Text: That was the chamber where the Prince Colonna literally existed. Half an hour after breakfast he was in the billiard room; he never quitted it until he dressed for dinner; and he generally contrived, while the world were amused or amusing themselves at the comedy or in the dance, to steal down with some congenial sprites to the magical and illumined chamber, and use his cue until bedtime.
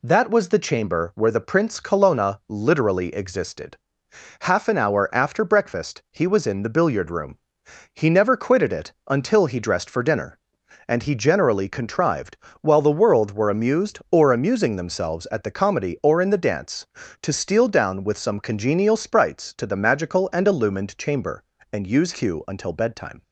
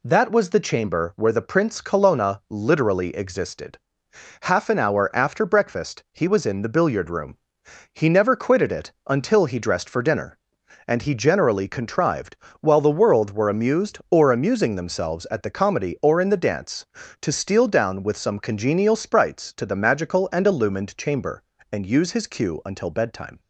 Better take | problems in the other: second | pauses between "it" and "until"; slight; at 8.9 s; 0.16 s long; slight in the second // skips "his"; at 22.1 s

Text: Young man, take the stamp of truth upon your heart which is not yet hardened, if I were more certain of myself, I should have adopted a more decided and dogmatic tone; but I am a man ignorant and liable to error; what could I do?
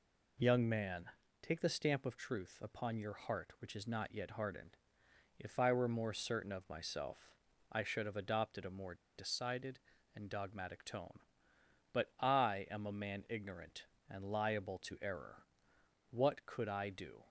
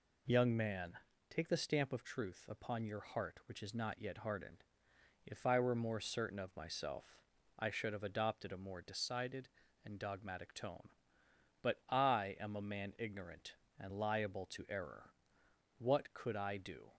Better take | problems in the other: second | pauses between "more" and "decided"; slight; at 8.9 s; 0.19 s long

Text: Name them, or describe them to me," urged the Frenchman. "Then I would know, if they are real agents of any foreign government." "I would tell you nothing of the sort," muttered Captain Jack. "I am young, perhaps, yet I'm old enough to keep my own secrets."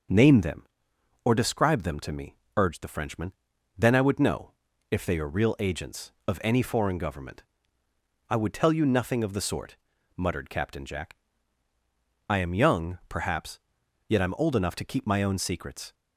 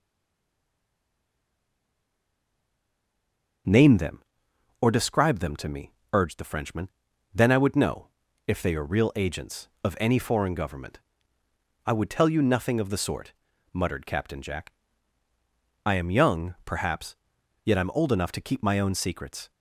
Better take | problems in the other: first | stays silent before the first word; strong; until 3.6 s; 3.6 s long // starts louder than the rest; until 5.2 s; 6.5 dB; also in the first

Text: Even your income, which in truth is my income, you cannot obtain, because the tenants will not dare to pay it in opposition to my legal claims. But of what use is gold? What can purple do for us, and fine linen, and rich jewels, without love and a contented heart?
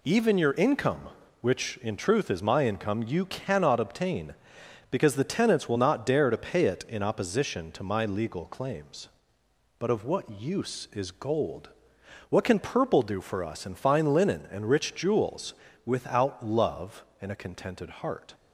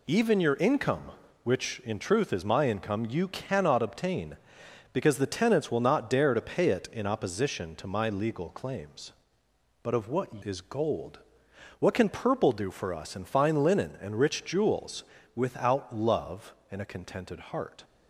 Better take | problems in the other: first | skips "use"; at 10.4 s

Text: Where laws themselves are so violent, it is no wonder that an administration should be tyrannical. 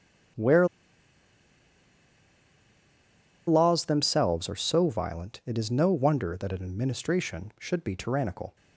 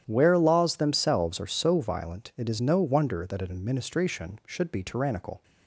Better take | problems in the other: second | starts louder than the rest; strong; until 4.1 s; 10.5 dB; strong in the second // pauses between "Where" and "laws"; strong; at 0.6 s; 2.8 s long

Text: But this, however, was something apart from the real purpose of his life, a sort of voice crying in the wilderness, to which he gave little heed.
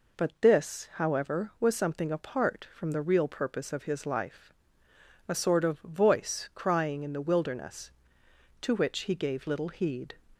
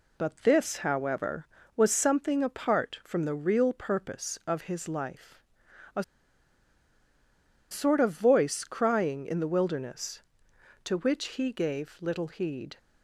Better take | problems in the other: first | pauses between "a" and "sort"; strong; at 6.0 s; 1.6 s long

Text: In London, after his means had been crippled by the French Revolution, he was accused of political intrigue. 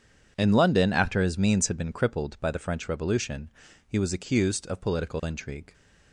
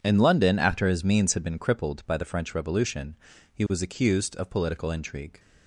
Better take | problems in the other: neither | none

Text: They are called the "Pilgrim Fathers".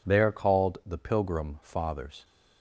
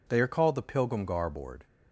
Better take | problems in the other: first | says "Garboard" for "Fathers"; at 1.0 s

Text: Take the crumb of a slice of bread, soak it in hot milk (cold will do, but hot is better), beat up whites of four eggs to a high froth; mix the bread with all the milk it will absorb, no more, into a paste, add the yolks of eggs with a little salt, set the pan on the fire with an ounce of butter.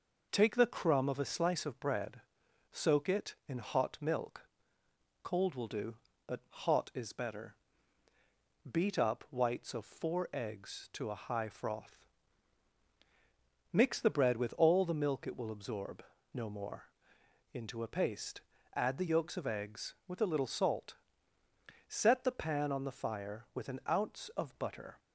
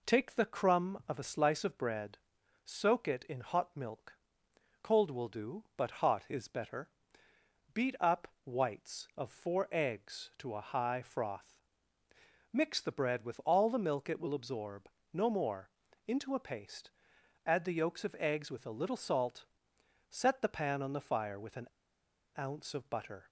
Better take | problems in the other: first | pauses between "up" and "whites"; slight; at 8.2 s; 0.16 s long // pauses between "an" and "ounce"; noticeable; at 21.6 s; 0.66 s long

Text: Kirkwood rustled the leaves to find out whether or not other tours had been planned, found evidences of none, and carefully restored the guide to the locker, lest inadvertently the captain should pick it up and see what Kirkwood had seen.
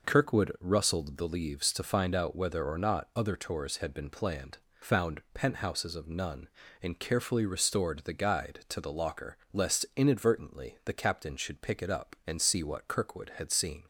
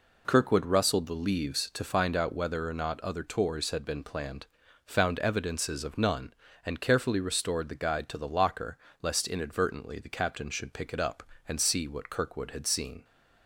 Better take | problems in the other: second | says "penthouses" for "evidences"; at 5.3 s

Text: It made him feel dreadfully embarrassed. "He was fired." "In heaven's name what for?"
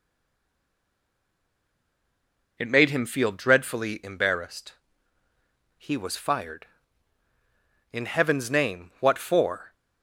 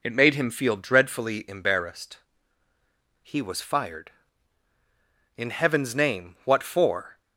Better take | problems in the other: second | stays silent before the first word; strong; until 2.5 s; 2.5 s long

